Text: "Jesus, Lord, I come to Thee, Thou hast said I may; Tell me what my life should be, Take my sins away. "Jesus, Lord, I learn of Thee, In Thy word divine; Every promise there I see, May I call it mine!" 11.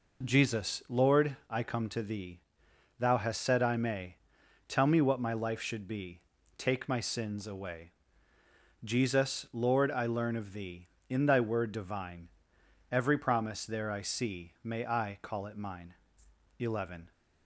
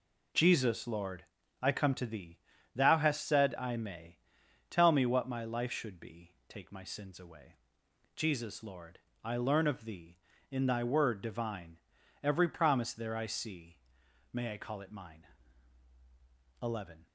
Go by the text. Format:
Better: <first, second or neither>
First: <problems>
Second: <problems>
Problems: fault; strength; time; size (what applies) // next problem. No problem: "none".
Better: neither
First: none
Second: none